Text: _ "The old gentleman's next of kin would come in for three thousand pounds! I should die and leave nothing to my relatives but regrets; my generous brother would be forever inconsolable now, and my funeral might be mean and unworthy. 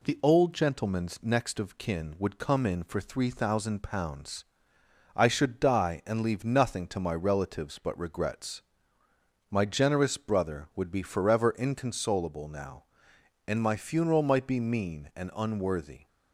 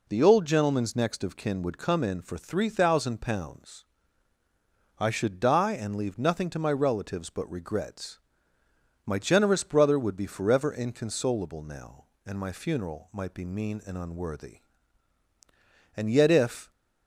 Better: first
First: none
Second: goes on to say "And yet if"; noticeable; from 15.9 s on; 0.74 s long

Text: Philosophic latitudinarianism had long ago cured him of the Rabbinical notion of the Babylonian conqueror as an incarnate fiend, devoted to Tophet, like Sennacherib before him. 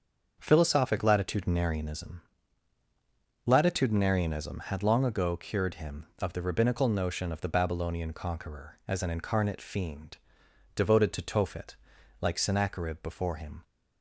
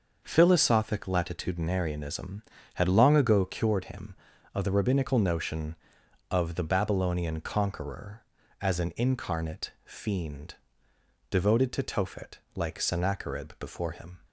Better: second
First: starts louder than the rest; until 1.3 s; 6.5 dB // says "latitudinarianism" twice; at 3.4 s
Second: starts louder than the rest; until 1.2 s; 6 dB

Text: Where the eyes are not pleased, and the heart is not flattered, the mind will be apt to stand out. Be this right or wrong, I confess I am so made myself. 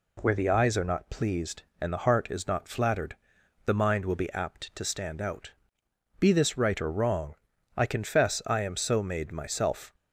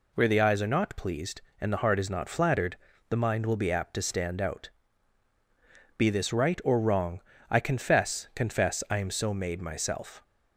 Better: first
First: none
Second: says "confess" twice; at 8.3 s

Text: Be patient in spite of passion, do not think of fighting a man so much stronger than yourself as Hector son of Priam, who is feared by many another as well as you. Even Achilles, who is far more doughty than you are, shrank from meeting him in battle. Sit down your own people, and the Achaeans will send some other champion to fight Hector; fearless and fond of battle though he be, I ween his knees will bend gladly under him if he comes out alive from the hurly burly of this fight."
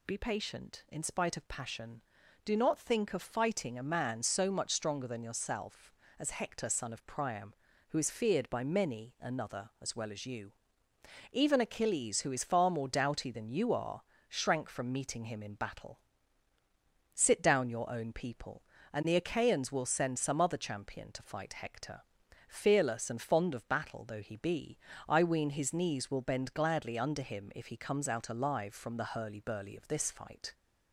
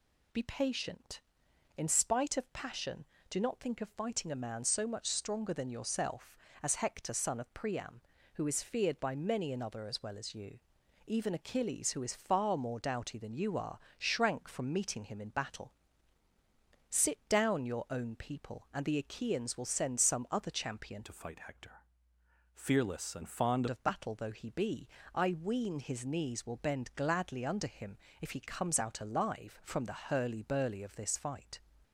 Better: first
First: none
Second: changes voice from "to" to "fond"; from 21.0 to 23.6 s; 2.6 s long // pauses between "him" and "if"; slight; at 27.9 s; 0.24 s long

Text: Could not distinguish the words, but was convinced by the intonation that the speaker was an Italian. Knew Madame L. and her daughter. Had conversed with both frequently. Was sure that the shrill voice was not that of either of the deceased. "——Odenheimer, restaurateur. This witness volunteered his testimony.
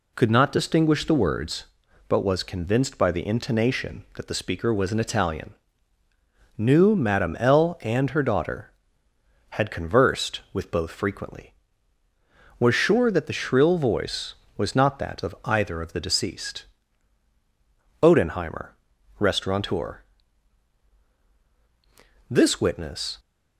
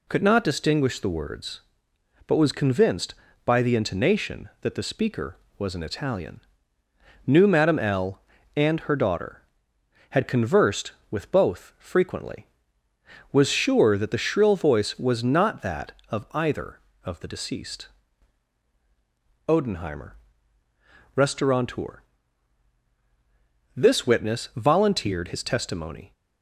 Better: second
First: stops before "volunteered his testimony"; at 23.1 s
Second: none

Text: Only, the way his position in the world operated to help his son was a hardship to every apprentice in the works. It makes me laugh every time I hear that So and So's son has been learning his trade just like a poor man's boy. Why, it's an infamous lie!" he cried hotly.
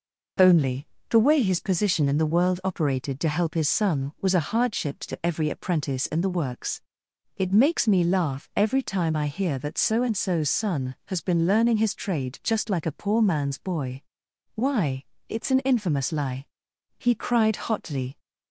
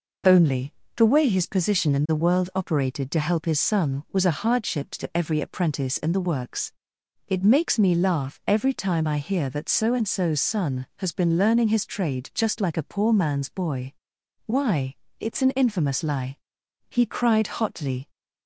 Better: neither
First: none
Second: none

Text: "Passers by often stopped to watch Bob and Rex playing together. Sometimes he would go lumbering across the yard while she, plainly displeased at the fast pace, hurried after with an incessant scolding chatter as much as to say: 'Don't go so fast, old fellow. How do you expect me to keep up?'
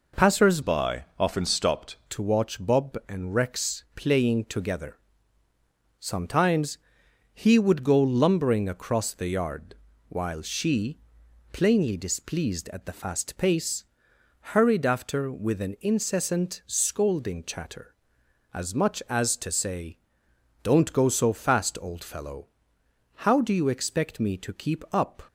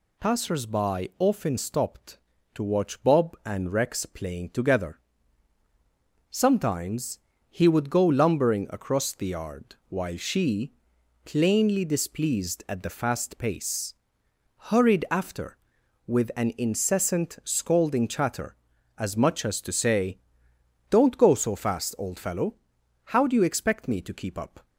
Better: second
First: changes voice from "by" to "stopped"; from 0.6 to 1.9 s; 1.3 s long // pauses between "Sometimes" and "he"; noticeable; at 6.7 s; 0.56 s long // pauses between "yard" and "while"; slight; at 9.7 s; 0.36 s long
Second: pauses between "Sometimes" and "he"; slight; at 7.1 s; 0.30 s long

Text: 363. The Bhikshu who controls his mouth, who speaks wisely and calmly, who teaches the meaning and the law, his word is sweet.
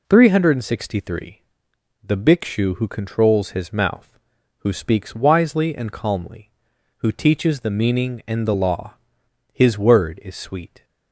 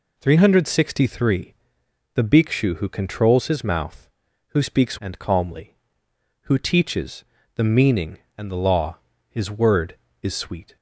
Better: first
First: none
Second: skips "wisely"; at 4.9 s // pauses between "teaches" and "the"; slight; at 7.2 s; 0.30 s long

